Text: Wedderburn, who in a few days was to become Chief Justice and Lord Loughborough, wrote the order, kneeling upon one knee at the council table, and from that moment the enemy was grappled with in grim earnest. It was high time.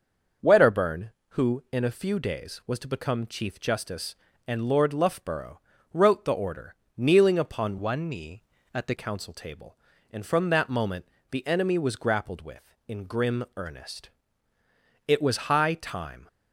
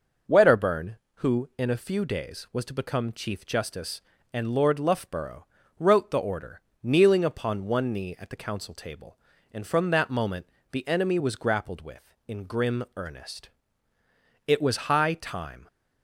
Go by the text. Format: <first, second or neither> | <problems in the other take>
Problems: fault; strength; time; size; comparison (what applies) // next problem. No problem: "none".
second | starts louder than the rest; noticeable; until 1.6 s; 6 dB // changes voice from "one" to "the"; from 7.7 to 8.9 s; 1.2 s long // pauses between "moment" and "the"; slight; at 11.0 s; 0.24 s long; slight in the second